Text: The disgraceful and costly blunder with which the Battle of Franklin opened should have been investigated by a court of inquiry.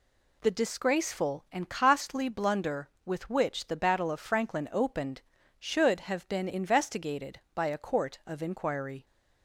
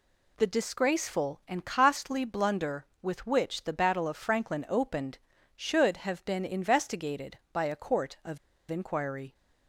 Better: first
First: none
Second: pauses between "of" and "inquiry"; slight; at 8.3 s; 0.33 s long

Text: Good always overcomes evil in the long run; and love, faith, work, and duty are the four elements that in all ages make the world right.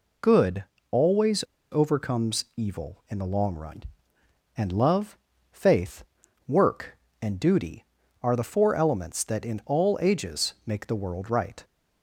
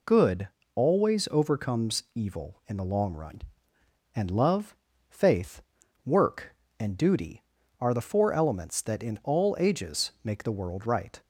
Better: second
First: pauses between "Good" and "always"; slight; at 0.6 s; 0.26 s long // pauses between "always" and "overcomes"; slight; at 1.4 s; 0.27 s long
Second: pauses between "Good" and "always"; slight; at 0.4 s; 0.26 s long

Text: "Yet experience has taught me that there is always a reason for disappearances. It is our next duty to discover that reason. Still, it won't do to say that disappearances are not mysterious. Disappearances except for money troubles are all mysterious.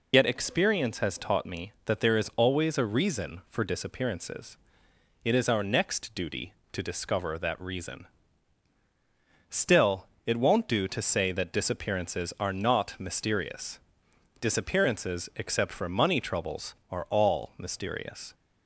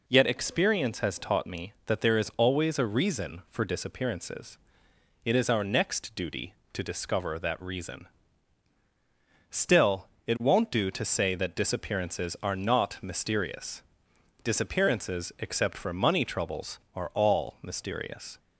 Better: second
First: loses the start of "Yet"; at 0.1 s; 60 ms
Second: none

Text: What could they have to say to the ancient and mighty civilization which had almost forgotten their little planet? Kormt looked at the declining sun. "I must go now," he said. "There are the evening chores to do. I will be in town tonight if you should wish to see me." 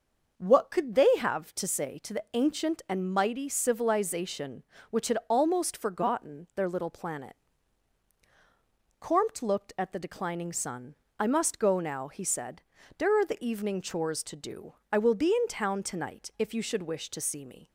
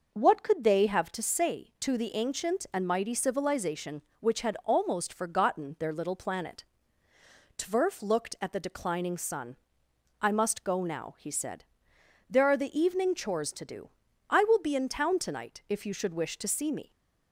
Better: first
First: none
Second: says "Tverf" for "Kormt"; at 7.5 s

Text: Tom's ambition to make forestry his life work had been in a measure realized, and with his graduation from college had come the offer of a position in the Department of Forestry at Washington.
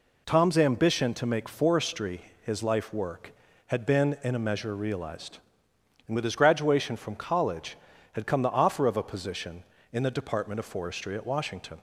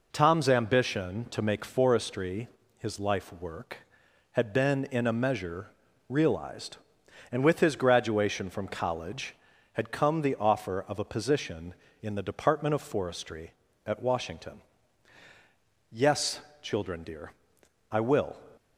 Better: first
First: pauses between "forestry" and "his"; slight; at 2.2 s; 0.20 s long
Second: pauses between "forestry" and "his"; slight; at 2.4 s; 0.30 s long // pauses between "measure" and "realized"; at 5.6 s; 0.40 s long // goes on to say "Yes children dear I will"; strong; from 15.9 s on; 2.4 s long

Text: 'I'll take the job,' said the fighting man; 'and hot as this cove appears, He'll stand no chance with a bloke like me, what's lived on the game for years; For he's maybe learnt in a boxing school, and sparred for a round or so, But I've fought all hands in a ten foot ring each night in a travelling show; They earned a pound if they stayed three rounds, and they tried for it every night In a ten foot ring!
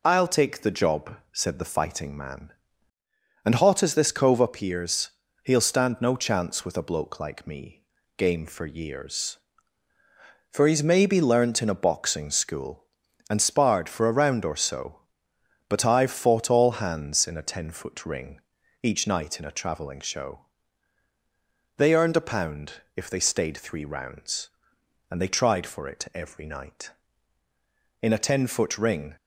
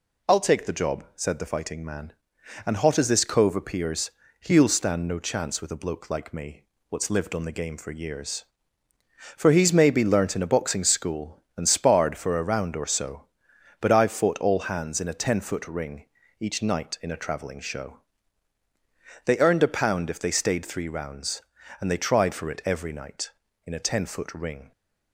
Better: second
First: skips "what's lived on the"; at 8.0 s // pauses between "ring" and "each"; at 18.3 s; 0.44 s long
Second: pauses between "ring" and "each"; slight; at 16.0 s; 0.34 s long

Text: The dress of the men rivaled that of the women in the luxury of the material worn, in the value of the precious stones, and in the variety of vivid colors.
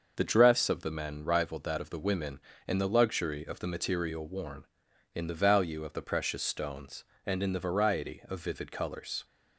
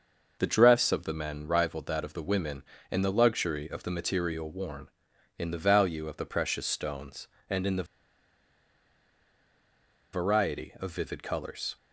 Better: first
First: starts louder than the rest; noticeable; until 1.2 s; 6 dB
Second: starts louder than the rest; noticeable; until 1.4 s; 6 dB // pauses between "the" and "variety"; strong; at 7.8 s; 2.2 s long

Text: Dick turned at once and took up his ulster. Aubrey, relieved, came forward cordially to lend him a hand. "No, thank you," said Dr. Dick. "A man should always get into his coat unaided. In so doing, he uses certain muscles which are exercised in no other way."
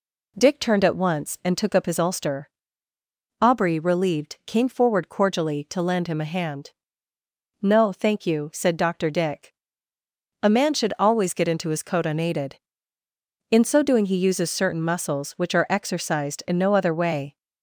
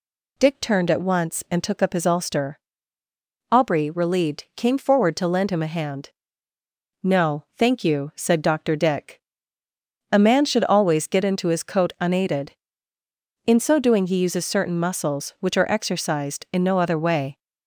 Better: first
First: none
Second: skips "cordially"; at 5.1 s

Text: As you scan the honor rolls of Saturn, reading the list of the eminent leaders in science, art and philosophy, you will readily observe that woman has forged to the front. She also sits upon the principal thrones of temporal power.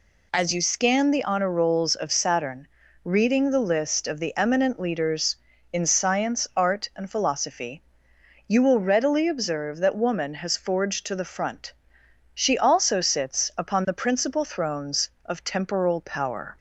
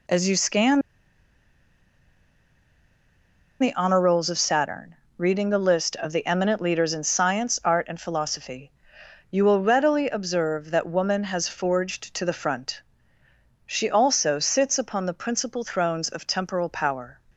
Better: first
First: none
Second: pauses between "scan" and "the"; strong; at 0.8 s; 2.8 s long

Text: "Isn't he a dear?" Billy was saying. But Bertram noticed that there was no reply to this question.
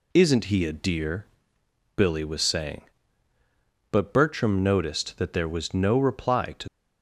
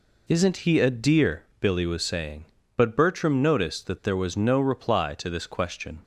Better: second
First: stops before "this question"; at 6.6 s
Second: none

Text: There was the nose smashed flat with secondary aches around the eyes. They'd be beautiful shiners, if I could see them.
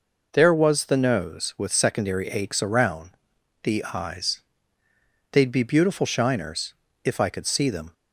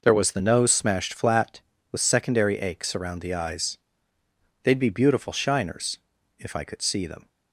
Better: second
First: skips "smashed flat"; at 1.5 s // pauses between "around" and "the"; noticeable; at 3.1 s; 0.54 s long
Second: none

